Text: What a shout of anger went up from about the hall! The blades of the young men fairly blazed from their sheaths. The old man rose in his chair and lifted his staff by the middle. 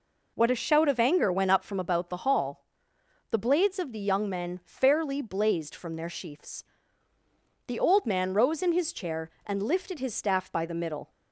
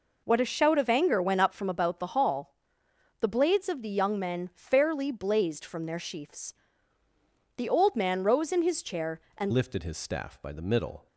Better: first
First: none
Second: changes voice at "lifted"; from 9.5 s on; 1.5 s long

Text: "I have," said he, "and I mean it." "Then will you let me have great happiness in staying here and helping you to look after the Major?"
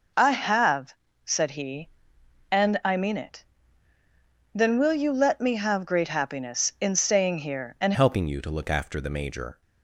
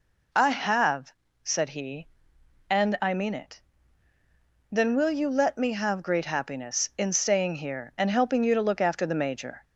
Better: second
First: changes voice at "helping"; from 7.9 s on; 1.7 s long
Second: none

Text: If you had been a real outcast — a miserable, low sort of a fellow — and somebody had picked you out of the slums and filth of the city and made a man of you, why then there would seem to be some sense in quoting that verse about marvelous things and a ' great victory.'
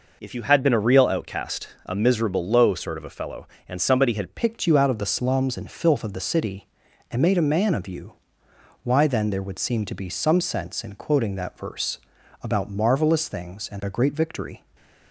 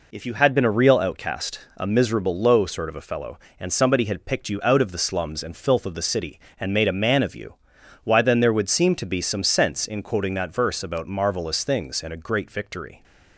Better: second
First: changes voice at "picked"; from 4.3 s on; 10.3 s long // pauses between "verse" and "about"; at 11.9 s; 0.42 s long // stays silent after the last word; slight; from 14.5 s on; 0.6 s long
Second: none

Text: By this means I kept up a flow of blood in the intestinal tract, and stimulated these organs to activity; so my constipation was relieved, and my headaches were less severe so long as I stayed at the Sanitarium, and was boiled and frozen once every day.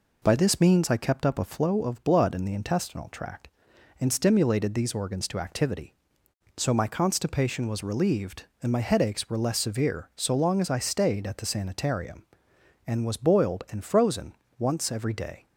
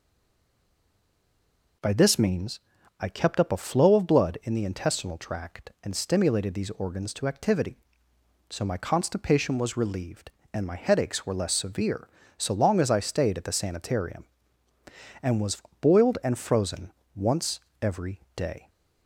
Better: first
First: pauses between "frozen" and "once"; slight; at 14.3 s; 0.24 s long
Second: stays silent before the first word; noticeable; until 1.8 s; 1.8 s long // pauses between "means" and "I"; at 2.5 s; 0.40 s long // pauses between "was" and "boiled"; slight; at 15.6 s; 0.20 s long // pauses between "frozen" and "once"; slight; at 16.9 s; 0.22 s long // pauses between "once" and "every"; slight; at 17.5 s; 0.24 s long

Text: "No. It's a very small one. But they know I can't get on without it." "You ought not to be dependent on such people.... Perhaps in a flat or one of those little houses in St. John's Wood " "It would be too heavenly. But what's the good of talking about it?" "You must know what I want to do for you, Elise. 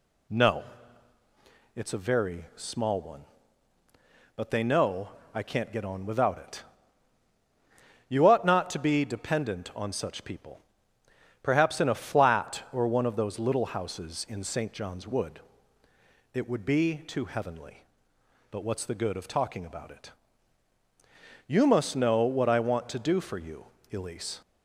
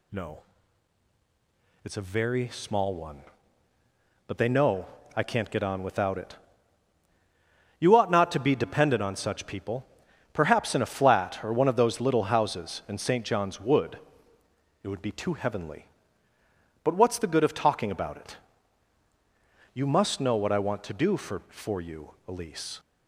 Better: first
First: pauses between "know" and "I"; slight; at 5.0 s; 0.24 s long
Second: pauses between "know" and "I"; slight; at 4.8 s; 0.30 s long // says "for" twice; at 21.4 s

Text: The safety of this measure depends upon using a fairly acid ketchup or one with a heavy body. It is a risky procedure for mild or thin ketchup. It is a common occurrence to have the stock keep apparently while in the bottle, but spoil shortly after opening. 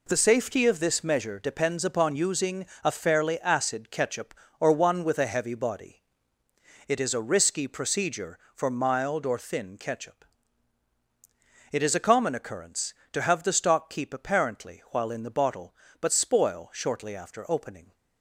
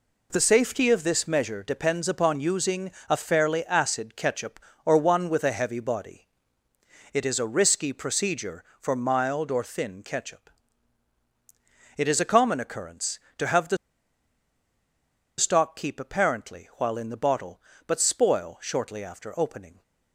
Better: first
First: pauses between "using" and "a"; slight; at 2.6 s; 0.18 s long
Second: pauses between "using" and "a"; slight; at 2.9 s; 0.18 s long // pauses between "the" and "stock"; strong; at 13.7 s; 1.6 s long

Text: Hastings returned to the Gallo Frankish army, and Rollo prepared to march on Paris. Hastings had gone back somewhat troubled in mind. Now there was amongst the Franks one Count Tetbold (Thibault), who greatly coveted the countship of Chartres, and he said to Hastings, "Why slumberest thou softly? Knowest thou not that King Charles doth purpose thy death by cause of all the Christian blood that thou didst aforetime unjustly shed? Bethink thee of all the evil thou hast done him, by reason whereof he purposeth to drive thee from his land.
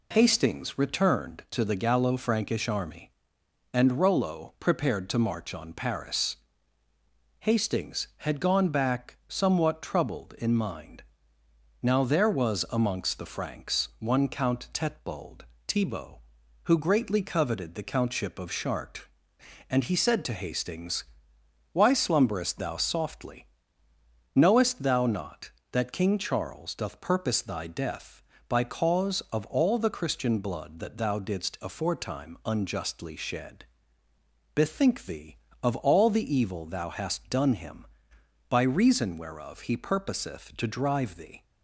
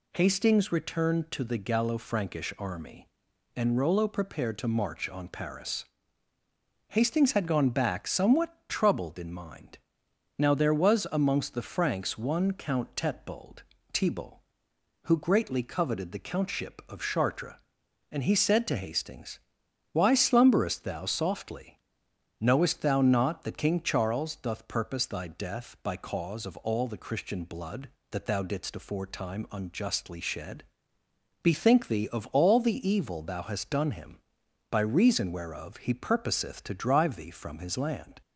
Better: second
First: stops before "from his land"; at 41.4 s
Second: none

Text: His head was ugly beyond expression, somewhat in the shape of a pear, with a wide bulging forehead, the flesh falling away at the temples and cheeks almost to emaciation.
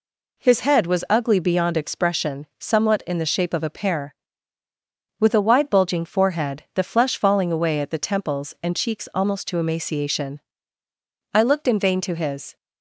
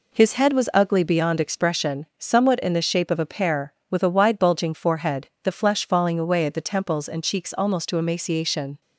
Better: second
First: goes on to say "I looked in vain to his"; noticeable; from 11.3 s on; 1.2 s long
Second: none

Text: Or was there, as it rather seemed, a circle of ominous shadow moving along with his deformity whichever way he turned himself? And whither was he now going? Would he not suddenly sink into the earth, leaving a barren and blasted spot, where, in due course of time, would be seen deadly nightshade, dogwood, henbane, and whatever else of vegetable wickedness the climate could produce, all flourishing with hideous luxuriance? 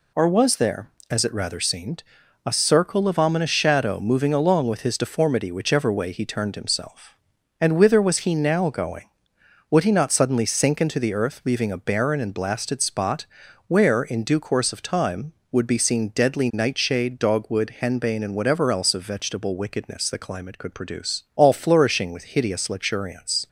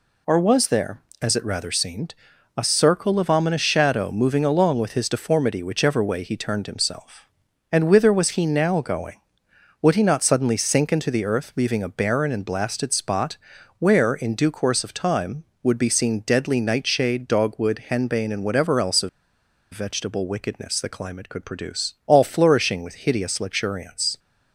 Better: first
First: none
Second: pauses between "of" and "vegetable"; noticeable; at 19.0 s; 0.63 s long

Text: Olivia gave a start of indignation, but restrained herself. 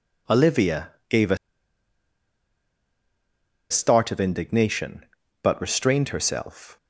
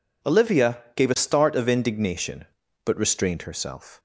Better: second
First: pauses between "Olivia" and "gave"; slight; at 0.8 s; 0.18 s long // pauses between "a" and "start"; strong; at 1.3 s; 2.3 s long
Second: none

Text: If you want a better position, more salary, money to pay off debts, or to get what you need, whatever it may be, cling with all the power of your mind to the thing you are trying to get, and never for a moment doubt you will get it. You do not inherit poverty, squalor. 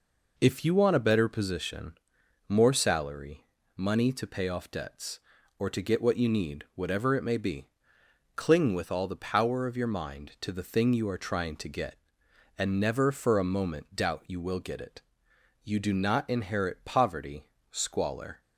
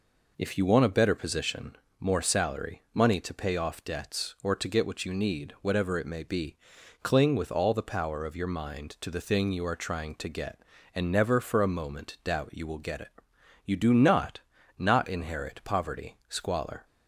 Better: first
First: none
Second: says "not" twice; at 14.7 s

